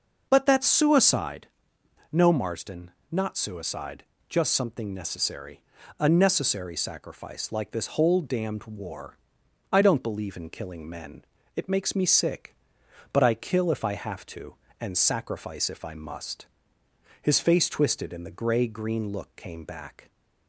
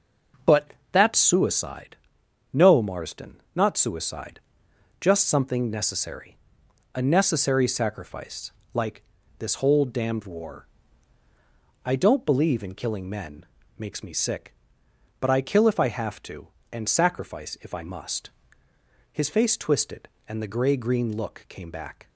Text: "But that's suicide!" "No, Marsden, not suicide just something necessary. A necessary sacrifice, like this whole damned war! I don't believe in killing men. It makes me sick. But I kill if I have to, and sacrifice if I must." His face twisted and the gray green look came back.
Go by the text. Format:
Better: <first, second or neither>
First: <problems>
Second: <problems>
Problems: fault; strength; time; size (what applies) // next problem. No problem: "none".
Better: first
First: pauses between "suicide" and "just"; slight; at 4.0 s; 0.26 s long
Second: pauses between "But" and "that's"; slight; at 0.7 s; 0.18 s long // pauses between "suicide" and "just"; noticeable; at 4.4 s; 0.60 s long // pauses between "like" and "this"; slight; at 9.0 s; 0.34 s long // skips "It"; at 13.6 s